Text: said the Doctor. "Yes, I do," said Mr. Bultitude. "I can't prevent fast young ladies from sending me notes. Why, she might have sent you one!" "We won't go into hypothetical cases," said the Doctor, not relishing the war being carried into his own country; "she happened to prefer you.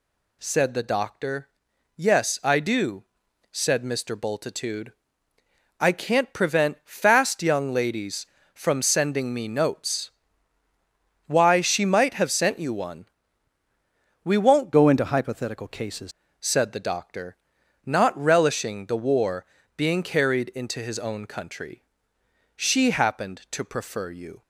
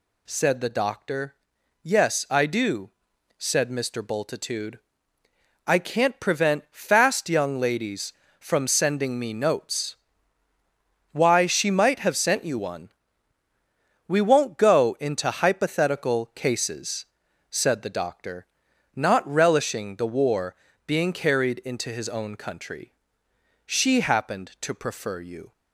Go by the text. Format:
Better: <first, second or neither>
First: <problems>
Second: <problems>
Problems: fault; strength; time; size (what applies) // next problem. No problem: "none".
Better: second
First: changes voice from "go" to "cases"; from 14.7 to 16.1 s; 1.4 s long // pauses between "war" and "being"; slight; at 19.4 s; 0.30 s long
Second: pauses between "war" and "being"; slight; at 20.5 s; 0.30 s long